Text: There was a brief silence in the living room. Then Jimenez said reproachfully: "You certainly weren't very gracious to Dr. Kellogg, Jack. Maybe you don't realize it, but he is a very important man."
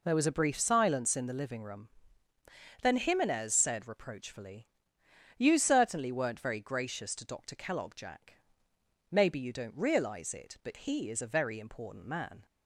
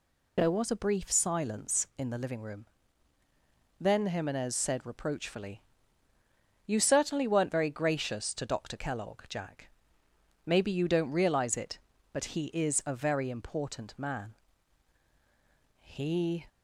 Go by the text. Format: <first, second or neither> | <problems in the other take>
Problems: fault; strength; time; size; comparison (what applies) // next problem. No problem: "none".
first | goes on to say "He"; noticeable; from 15.8 s on; 0.64 s long